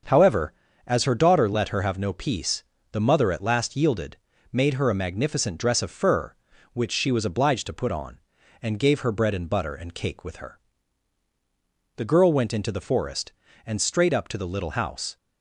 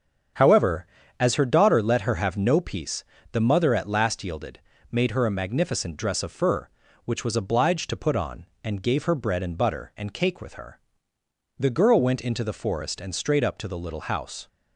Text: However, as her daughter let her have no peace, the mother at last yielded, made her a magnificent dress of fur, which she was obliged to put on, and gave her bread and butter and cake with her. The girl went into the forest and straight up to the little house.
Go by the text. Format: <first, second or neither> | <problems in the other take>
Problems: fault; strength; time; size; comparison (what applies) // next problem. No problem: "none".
first | starts louder than the rest; strong; until 1.7 s; 7.5 dB; also in the first // skips "she"; at 7.2 s